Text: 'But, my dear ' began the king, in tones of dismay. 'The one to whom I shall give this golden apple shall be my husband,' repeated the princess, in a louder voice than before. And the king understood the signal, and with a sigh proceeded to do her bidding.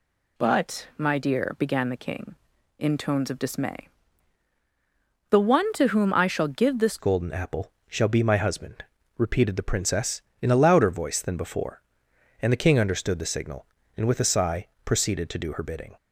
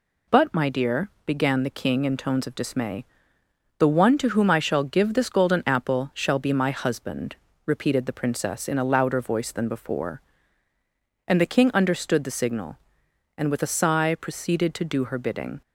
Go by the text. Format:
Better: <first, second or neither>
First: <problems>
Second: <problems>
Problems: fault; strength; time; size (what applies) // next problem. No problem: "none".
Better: second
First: changes voice at "golden"; from 6.9 s on; 9.0 s long // pauses between "apple" and "shall"; slight; at 7.7 s; 0.16 s long // pauses between "sigh" and "proceeded"; slight; at 14.6 s; 0.18 s long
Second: none